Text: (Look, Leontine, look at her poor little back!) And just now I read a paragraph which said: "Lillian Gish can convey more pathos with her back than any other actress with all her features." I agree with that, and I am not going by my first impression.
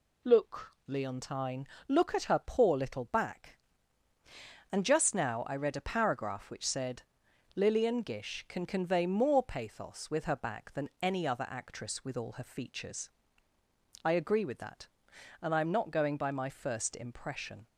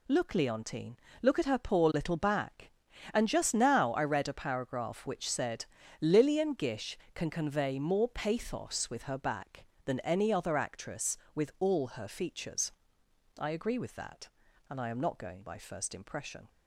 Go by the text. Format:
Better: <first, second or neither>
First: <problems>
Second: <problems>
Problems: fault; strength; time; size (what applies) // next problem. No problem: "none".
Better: first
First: none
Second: skips "my"; at 15.5 s